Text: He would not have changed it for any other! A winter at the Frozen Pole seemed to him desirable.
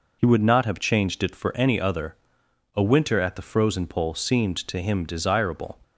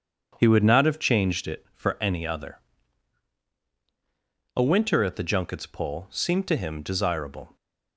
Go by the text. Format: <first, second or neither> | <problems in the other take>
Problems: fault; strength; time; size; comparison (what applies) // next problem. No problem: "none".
first | starts louder than the rest; strong; until 1.4 s; 7.5 dB // says "Junkets" for "Frozen"; at 5.2 s